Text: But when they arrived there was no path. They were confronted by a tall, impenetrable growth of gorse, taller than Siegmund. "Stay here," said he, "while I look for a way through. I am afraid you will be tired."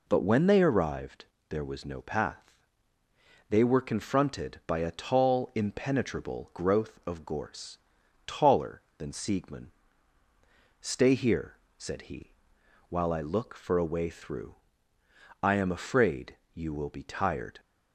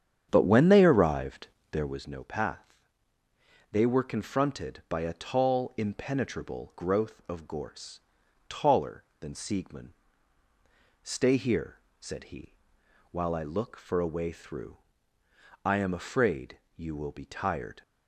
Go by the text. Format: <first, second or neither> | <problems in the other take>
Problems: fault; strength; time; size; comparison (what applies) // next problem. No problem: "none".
first | starts louder than the rest; strong; until 2.1 s; 8.5 dB // pauses between "arrived" and "there"; slight; at 1.4 s; 0.24 s long; slight in the first // pauses between "afraid" and "you"; slight; at 16.5 s; 0.16 s long; slight in the first